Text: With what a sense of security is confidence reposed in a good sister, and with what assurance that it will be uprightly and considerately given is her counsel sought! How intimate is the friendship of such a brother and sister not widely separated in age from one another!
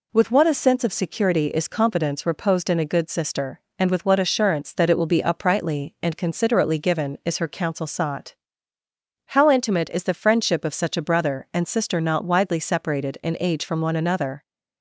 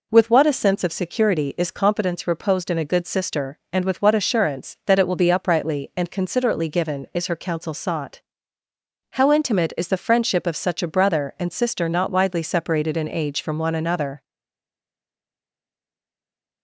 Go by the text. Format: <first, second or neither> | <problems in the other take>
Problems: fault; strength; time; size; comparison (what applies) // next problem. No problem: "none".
first | stays silent after the last word; from 14.2 s on; 2.4 s long